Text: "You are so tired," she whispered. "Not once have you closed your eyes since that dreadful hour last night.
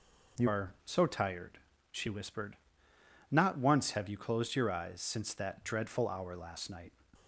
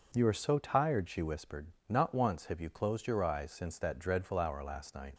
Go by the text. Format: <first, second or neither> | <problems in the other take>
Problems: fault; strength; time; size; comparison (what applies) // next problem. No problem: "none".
second | changes voice at "are"; from 0.4 s on; 6.5 s long